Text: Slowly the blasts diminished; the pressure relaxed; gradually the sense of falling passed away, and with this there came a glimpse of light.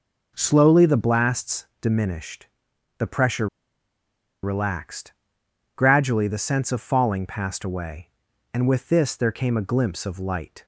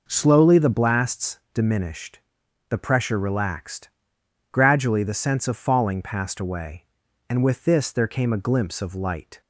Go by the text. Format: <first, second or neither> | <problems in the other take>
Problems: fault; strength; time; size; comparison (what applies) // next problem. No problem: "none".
second | pauses between "pressure" and "relaxed"; noticeable; at 3.4 s; 0.96 s long